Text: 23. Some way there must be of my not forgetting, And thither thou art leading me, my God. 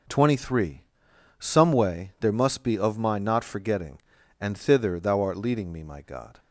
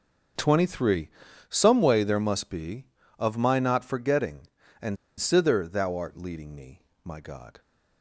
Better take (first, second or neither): first